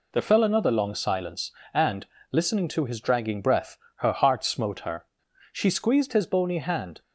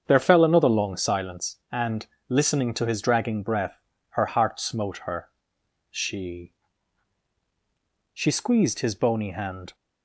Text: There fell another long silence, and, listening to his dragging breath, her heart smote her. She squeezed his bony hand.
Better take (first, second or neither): first